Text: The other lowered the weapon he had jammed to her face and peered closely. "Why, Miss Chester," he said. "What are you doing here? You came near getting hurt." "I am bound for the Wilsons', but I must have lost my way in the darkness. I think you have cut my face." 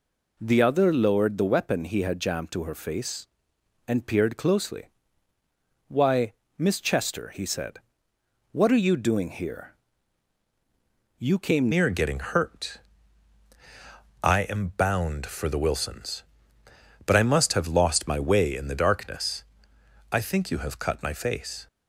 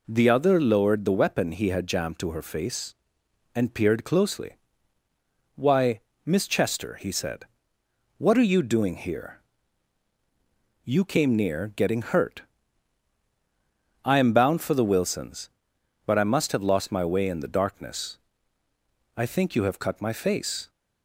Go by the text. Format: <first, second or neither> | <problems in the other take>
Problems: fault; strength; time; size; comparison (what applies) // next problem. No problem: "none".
second | changes voice at "near"; from 11.7 s on; 9.9 s long